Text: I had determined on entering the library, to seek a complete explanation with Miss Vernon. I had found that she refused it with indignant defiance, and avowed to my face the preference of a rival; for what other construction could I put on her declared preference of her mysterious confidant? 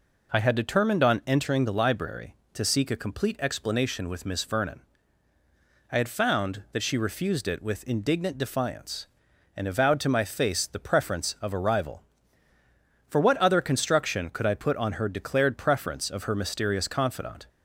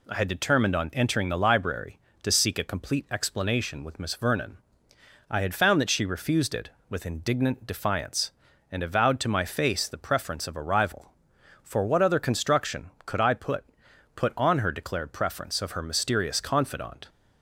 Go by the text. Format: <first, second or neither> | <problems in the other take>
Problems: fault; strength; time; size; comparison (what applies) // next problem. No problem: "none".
first | says "put" twice; at 14.1 s